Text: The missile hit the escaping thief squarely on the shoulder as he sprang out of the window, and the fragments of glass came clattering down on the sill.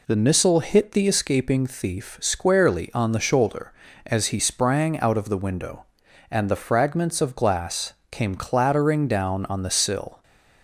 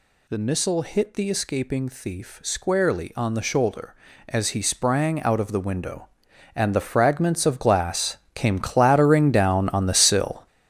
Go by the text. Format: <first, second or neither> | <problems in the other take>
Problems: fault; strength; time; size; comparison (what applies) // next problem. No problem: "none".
first | gets louder; strong; throughout; 9.5 dB // pauses between "glass" and "came"; slight; at 8.1 s; 0.18 s long; slight in the first